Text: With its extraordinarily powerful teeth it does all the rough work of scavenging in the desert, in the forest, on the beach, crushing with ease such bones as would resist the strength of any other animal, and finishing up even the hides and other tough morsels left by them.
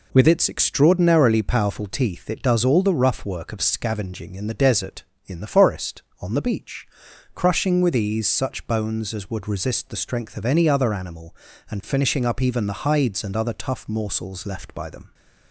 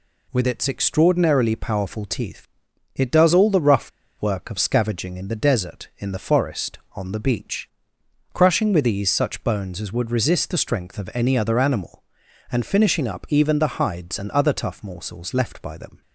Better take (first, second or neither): first